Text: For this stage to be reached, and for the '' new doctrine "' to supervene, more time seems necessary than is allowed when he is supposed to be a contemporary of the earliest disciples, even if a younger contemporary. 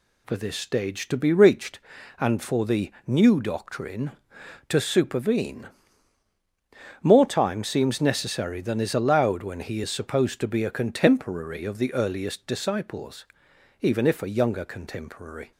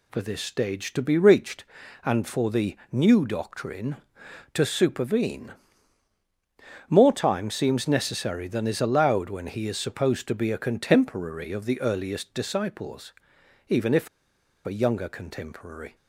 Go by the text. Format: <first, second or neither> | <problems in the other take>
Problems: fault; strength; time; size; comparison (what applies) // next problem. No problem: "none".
first | pauses between "if" and "a"; noticeable; at 14.0 s; 0.58 s long